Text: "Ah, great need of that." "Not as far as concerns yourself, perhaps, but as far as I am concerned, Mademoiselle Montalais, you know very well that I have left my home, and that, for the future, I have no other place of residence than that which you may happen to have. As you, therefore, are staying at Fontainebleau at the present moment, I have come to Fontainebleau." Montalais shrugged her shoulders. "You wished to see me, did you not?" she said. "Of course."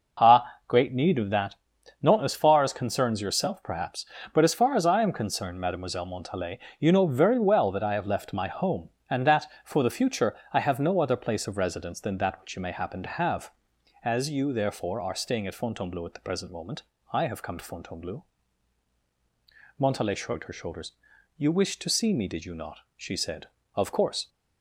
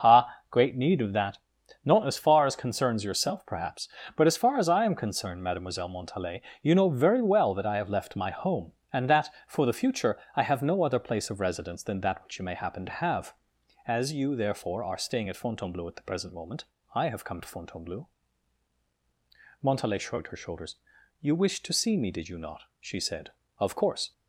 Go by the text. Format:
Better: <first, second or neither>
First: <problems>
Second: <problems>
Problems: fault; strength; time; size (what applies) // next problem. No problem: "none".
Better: neither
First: none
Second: none